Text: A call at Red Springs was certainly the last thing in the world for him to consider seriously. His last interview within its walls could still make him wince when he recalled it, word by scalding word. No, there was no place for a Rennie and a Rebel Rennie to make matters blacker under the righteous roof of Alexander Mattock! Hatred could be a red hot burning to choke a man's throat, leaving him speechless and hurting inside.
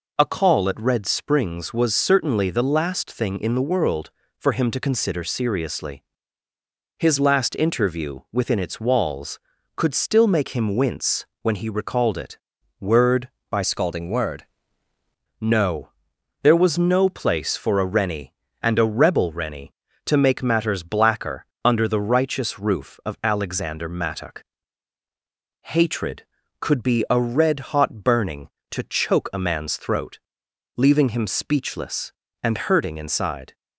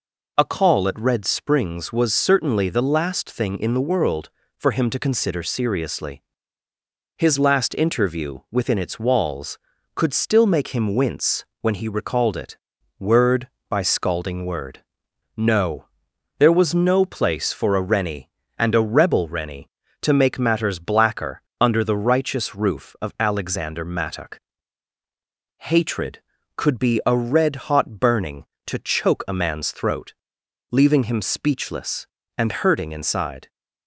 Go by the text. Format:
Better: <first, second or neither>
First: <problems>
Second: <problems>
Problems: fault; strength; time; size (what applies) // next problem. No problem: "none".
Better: second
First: pauses between "wince" and "when"; slight; at 11.2 s; 0.16 s long // changes voice from "scalding" to "word"; from 13.6 to 14.4 s; 0.8 s long // pauses between "blacker" and "under"; slight; at 21.4 s; 0.18 s long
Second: pauses between "wince" and "when"; slight; at 11.4 s; 0.16 s long // pauses between "blacker" and "under"; slight; at 21.4 s; 0.18 s long